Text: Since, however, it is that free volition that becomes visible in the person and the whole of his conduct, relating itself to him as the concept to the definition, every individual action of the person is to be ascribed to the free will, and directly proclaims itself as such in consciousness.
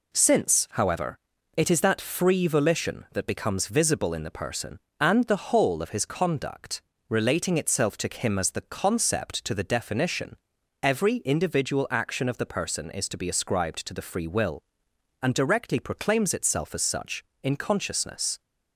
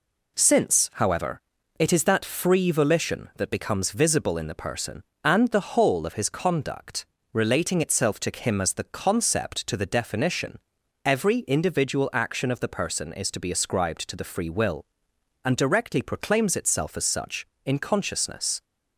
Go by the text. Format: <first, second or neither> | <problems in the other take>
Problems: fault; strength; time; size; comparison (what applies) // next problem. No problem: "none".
neither | none